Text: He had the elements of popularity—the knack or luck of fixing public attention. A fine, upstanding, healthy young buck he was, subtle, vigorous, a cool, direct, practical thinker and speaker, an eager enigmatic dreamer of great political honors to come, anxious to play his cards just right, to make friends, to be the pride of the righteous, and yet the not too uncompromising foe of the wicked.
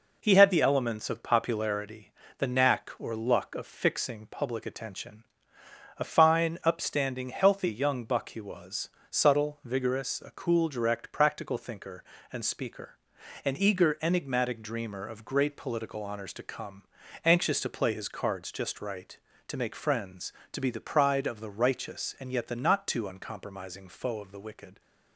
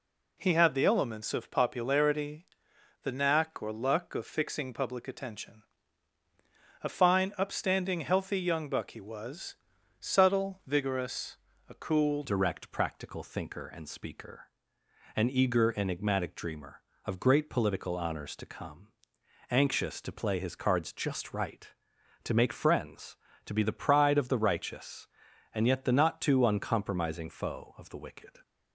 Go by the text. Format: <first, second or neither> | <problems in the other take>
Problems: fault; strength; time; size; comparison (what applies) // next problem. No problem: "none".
first | changes voice at "direct"; from 12.2 s on; 16.1 s long